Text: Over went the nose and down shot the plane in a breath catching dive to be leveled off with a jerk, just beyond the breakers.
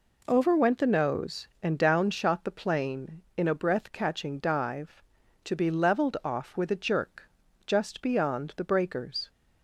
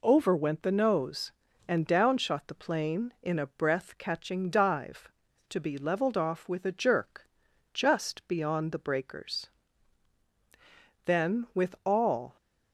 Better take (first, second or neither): first